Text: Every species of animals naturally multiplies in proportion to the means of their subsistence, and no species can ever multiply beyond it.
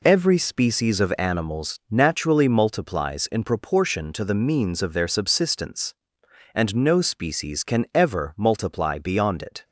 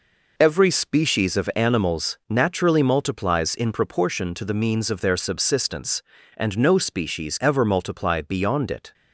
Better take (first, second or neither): first